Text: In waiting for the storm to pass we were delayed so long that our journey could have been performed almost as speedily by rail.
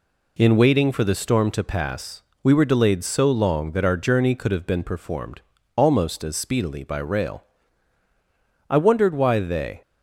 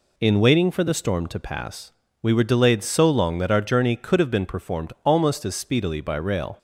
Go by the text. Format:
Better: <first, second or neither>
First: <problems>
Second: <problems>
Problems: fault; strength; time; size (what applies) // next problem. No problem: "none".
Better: second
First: pauses between "pass" and "we"; slight; at 2.2 s; 0.22 s long // pauses between "performed" and "almost"; slight; at 5.4 s; 0.34 s long // goes on to say "I wondered why they"; noticeable; from 8.6 s on; 1.1 s long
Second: pauses between "pass" and "we"; slight; at 1.9 s; 0.30 s long